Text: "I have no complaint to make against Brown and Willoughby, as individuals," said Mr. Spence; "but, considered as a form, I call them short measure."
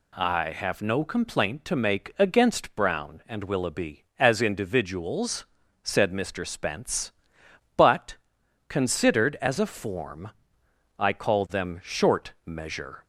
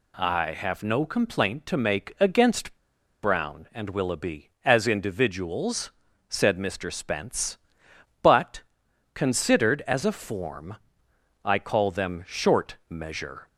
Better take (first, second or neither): first